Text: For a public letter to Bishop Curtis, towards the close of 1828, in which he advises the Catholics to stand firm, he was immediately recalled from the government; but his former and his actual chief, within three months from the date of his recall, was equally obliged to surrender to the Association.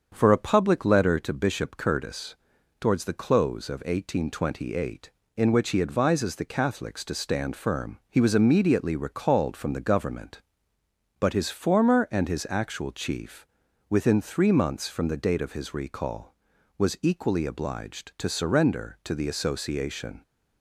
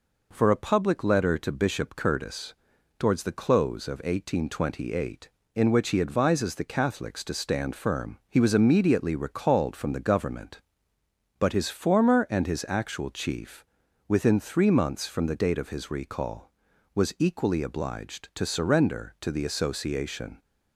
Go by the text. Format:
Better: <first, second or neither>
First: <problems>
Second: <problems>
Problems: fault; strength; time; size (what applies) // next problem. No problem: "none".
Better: second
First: starts louder than the rest; until 1.2 s; 7 dB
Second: none